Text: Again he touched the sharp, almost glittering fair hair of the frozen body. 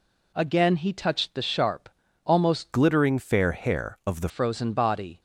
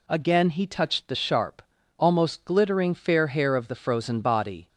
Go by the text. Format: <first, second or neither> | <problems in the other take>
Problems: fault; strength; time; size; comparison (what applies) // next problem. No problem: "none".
second | changes voice from "glittering" to "the"; from 2.7 to 4.2 s; 1.5 s long